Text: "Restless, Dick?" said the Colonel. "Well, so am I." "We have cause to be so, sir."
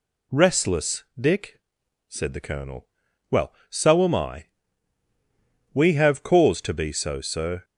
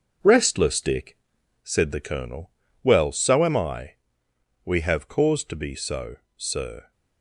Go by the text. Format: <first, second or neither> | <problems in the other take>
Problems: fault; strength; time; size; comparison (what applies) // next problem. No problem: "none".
first | gets quieter; noticeable; throughout; 5.5 dB